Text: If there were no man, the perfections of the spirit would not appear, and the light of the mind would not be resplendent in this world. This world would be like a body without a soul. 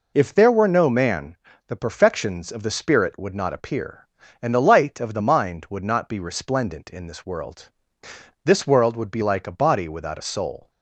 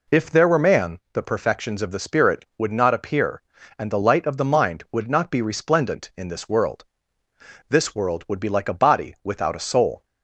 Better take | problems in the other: first | skips "no"; at 0.5 s

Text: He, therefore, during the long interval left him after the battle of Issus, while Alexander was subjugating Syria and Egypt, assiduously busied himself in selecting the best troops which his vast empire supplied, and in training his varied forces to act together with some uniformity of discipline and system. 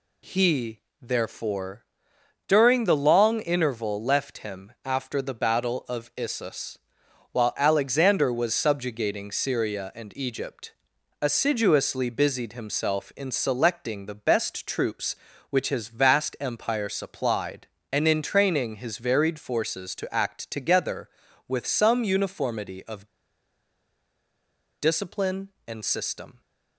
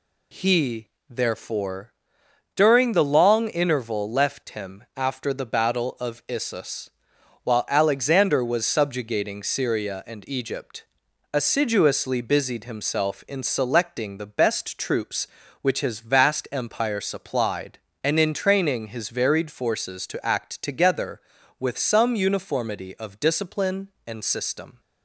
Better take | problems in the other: second | pauses between "of" and "discipline"; strong; at 23.0 s; 1.7 s long

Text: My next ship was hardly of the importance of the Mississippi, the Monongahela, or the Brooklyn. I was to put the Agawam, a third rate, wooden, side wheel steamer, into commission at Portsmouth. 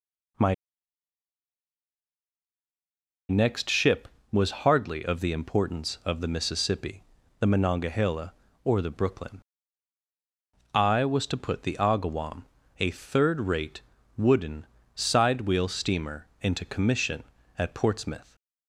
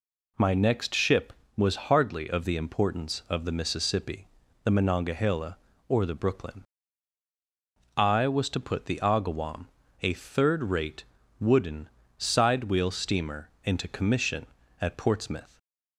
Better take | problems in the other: second | pauses between "My" and "next"; strong; at 0.5 s; 2.7 s long

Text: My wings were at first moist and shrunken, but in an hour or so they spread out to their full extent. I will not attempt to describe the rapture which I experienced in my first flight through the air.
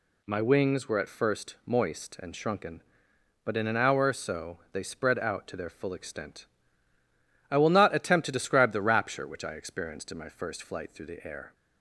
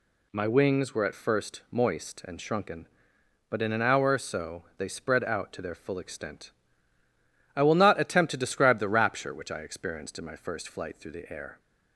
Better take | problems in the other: neither | none

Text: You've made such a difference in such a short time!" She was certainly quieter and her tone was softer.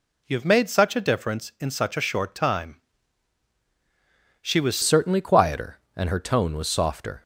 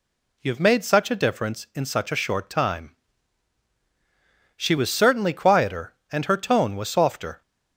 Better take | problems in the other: second | changes voice at "certainly"; from 4.8 s on; 2.4 s long

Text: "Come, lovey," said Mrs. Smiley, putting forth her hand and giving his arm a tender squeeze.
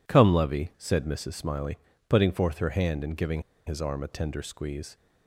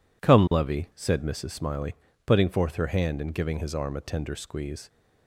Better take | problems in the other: second | pauses between "giving" and "his"; slight; at 3.4 s; 0.25 s long

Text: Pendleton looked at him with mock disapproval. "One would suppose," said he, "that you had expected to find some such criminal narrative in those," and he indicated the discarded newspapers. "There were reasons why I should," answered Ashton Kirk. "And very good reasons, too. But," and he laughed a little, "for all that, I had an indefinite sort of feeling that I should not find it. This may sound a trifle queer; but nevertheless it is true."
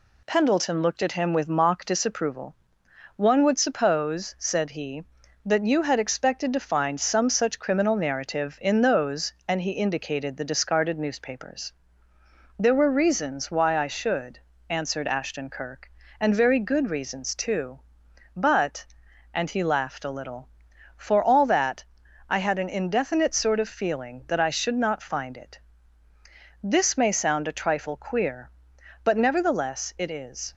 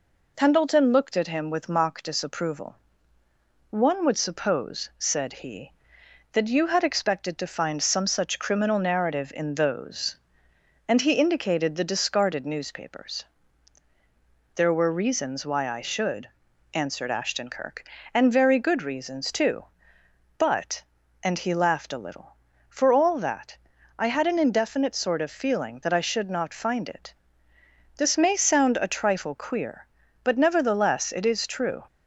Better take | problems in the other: second | stops before "true"; at 30.5 s

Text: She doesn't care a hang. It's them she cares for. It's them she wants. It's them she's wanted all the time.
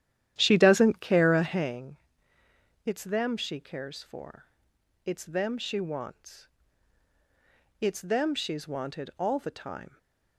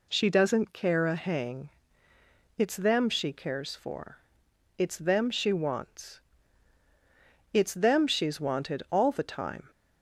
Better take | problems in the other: second | starts louder than the rest; strong; until 1.8 s; 11 dB // stays silent after the last word; slight; from 9.8 s on; 0.5 s long

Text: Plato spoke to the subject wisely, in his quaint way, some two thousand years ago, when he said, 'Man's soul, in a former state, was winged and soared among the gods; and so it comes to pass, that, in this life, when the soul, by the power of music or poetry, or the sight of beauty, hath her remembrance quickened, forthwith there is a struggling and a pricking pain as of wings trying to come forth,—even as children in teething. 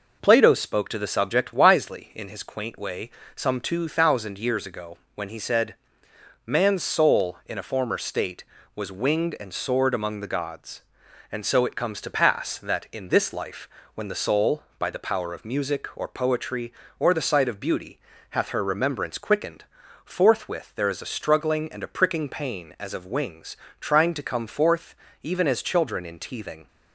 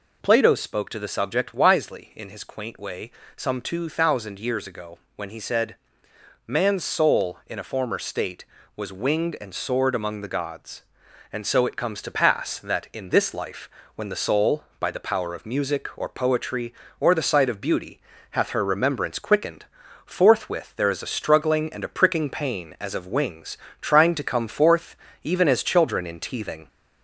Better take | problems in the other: first | gets louder; slight; throughout; 2.5 dB // pauses between "wings" and "trying"; slight; at 23.5 s; 0.22 s long; slight in the first

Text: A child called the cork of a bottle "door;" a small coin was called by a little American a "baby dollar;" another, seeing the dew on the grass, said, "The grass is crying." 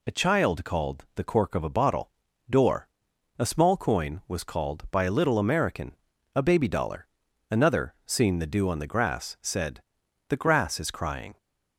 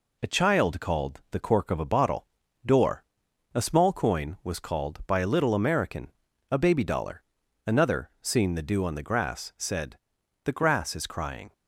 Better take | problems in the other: first | gets quieter; slight; throughout; 2.5 dB // pauses between "bottle" and "door"; at 2.2 s; 0.38 s long; also in the first // pauses between "American" and "a"; at 6.1 s; 0.40 s long; also in the first

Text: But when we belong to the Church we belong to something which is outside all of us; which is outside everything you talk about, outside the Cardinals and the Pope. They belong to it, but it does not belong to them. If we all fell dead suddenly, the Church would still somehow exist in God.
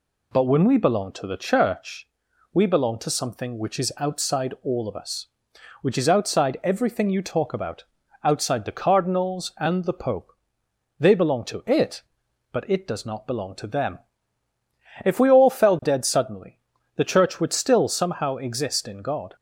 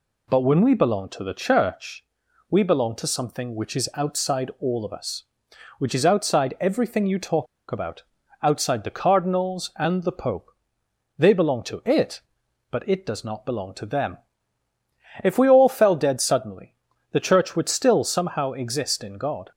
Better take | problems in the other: first | pauses between "Church" and "we"; noticeable; at 2.0 s; 0.48 s long; noticeable in the first // pauses between "talk" and "about"; slight; at 7.4 s; 0.24 s long

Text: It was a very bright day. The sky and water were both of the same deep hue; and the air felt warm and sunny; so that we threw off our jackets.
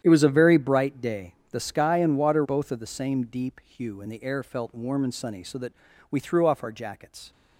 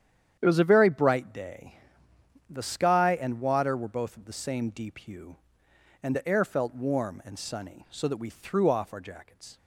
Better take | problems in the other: second | starts louder than the rest; strong; until 1.0 s; 10 dB; strong in the second // skips "were"; at 2.4 s // pauses between "that" and "we"; at 5.7 s; 0.40 s long

